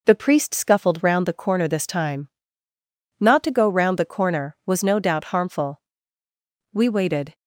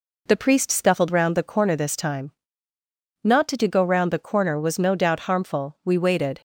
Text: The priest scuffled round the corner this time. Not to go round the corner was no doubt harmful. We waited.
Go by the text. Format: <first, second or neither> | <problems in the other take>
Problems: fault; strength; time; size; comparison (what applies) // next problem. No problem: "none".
first | says "to" twice; at 3.5 s